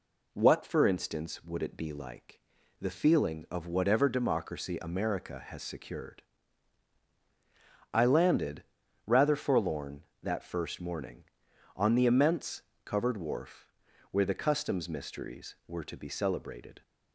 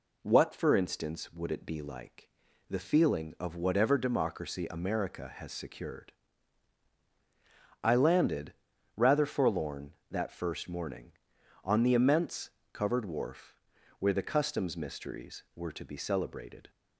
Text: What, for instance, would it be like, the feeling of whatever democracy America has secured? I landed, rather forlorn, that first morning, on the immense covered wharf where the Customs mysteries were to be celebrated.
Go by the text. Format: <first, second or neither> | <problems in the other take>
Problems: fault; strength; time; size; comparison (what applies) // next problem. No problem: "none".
neither | pauses between "immense" and "covered"; slight; the same in both // pauses between "wharf" and "where"; noticeable; the same in both